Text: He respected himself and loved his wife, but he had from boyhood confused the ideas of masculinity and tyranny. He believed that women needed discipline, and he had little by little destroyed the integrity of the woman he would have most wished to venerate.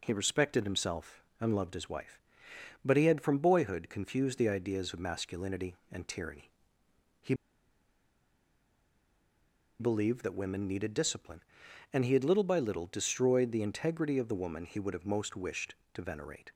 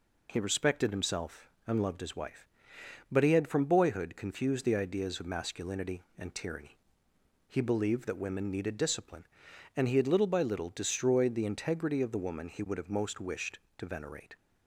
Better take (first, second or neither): second